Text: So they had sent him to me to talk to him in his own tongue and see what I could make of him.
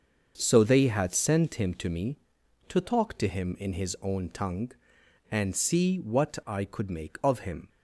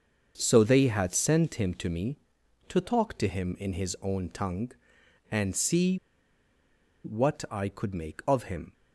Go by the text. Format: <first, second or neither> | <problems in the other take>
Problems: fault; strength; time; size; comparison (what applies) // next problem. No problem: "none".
first | starts louder than the rest; until 1.3 s; 6.5 dB; also in the first // pauses between "see" and "what"; at 5.9 s; 1.0 s long